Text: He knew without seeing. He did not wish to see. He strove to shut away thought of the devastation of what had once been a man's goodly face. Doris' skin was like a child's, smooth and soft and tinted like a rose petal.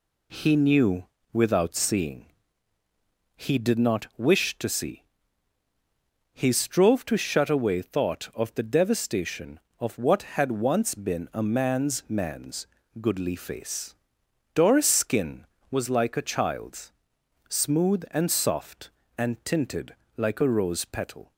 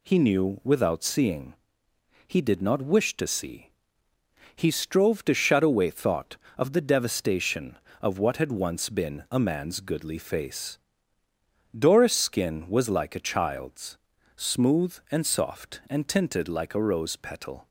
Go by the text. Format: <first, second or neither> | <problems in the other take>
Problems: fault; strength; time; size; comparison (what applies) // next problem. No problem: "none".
second | pauses between "knew" and "without"; slight; at 1.0 s; 0.26 s long // says "man's" twice; at 12.0 s // pauses between "tinted" and "like"; slight; at 19.9 s; 0.20 s long